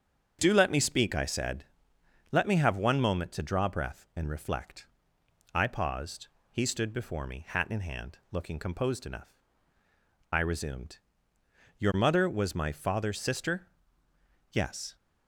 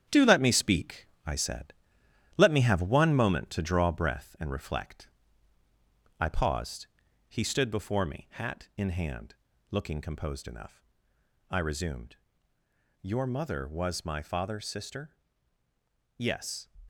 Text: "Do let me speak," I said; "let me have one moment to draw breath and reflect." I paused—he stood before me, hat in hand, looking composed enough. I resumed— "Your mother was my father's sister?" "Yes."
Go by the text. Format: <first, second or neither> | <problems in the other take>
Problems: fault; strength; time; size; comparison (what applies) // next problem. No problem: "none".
first | gets quieter; strong; throughout; 7.5 dB // starts louder than the rest; strong; until 1.3 s; 9.5 dB; strong in the first